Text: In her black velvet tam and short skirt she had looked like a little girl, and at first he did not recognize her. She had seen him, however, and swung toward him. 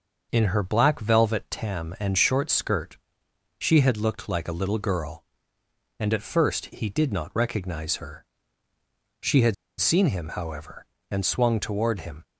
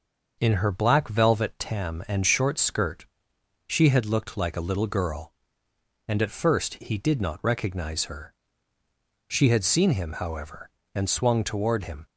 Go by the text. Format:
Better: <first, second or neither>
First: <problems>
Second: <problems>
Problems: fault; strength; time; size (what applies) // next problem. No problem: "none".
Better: second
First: starts louder than the rest; noticeable; until 1.3 s; 6 dB // pauses between "skirt" and "she"; noticeable; at 2.9 s; 0.60 s long // pauses between "had" and "seen"; slight; at 9.5 s; 0.26 s long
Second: starts louder than the rest; until 1.4 s; 6 dB // pauses between "skirt" and "she"; noticeable; at 3.0 s; 0.60 s long